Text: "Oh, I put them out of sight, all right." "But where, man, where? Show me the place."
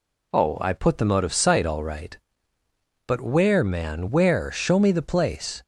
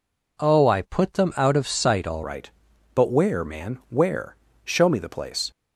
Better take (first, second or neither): first